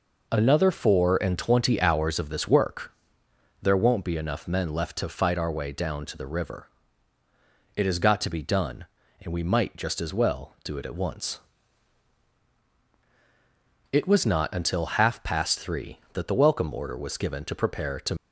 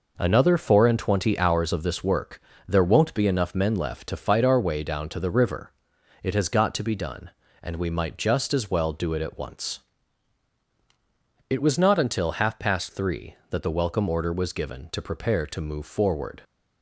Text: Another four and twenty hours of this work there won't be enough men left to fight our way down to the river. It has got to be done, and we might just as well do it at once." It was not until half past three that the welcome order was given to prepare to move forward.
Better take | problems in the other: second | pauses between "work" and "there"; noticeable; at 2.9 s; 0.70 s long; slight in the second // stops before "move forward"; at 18.1 s

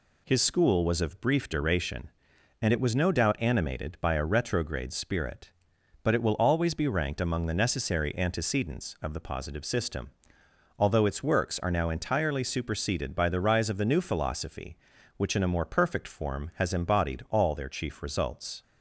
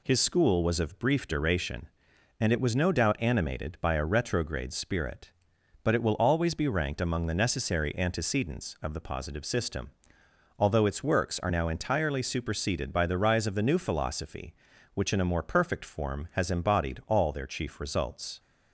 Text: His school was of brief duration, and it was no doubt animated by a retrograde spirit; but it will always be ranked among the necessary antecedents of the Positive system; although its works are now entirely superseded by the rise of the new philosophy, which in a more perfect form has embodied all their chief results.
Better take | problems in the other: neither | none

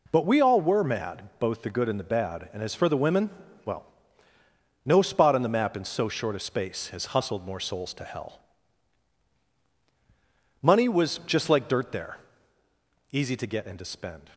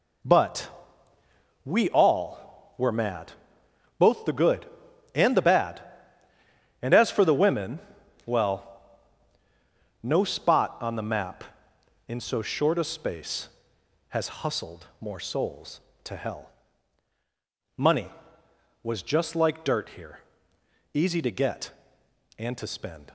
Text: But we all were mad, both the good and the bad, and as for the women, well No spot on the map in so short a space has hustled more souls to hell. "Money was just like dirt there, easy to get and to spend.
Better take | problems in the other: first | pauses between "But" and "we"; noticeable; at 0.6 s; 0.96 s long // pauses between "well" and "No"; strong; at 8.6 s; 1.3 s long; also in the first // says "here" for "there"; at 19.9 s

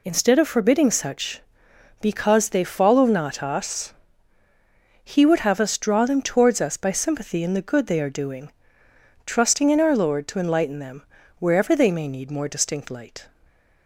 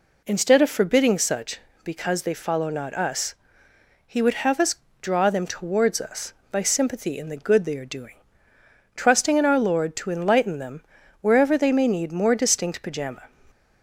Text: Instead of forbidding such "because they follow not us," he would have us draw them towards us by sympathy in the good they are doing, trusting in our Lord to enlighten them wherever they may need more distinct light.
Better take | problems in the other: first | pauses between "us" and "draw"; slight; at 4.7 s; 0.24 s long // pauses between "them" and "wherever"; at 10.8 s; 0.40 s long; slight in the first // says "pajama" for "light"; at 12.8 s

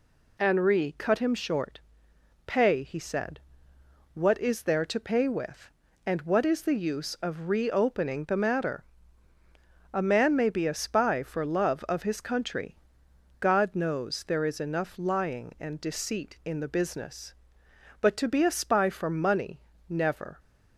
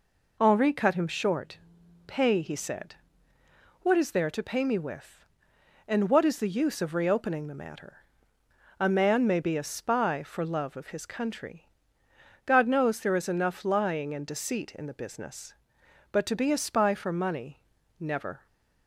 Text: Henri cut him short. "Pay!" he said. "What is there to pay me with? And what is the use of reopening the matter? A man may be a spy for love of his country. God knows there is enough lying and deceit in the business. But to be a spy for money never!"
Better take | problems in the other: second | skips "me"; at 5.2 s // pauses between "money" and "never"; slight; at 19.5 s; 0.30 s long; slight in the second

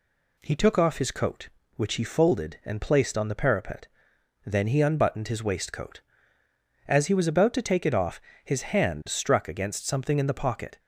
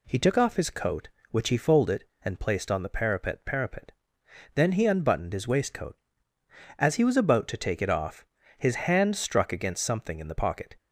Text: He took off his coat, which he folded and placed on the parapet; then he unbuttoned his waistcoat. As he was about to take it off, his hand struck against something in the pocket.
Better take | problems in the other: first | says "parapet" twice; at 3.4 s

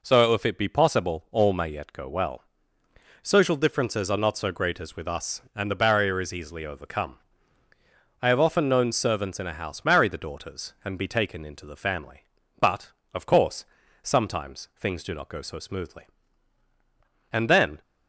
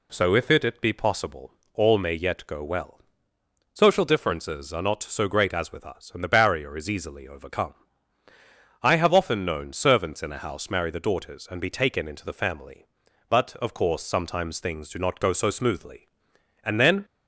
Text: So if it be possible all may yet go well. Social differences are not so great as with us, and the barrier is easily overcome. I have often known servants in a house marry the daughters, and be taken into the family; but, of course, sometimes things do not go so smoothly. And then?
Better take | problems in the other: first | says "it" twice; at 0.6 s // pauses between "possible" and "all"; slight; at 1.5 s; 0.20 s long

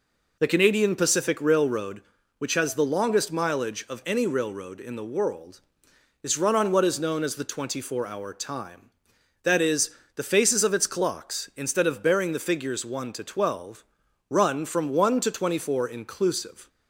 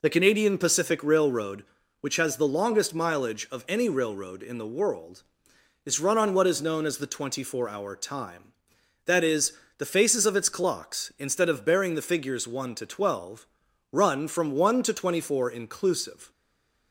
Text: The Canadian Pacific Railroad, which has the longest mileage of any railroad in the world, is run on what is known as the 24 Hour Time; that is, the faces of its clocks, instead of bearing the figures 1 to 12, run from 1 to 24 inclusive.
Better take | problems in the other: first | stays silent after the last word; slight; from 16.3 s on; 0.6 s long

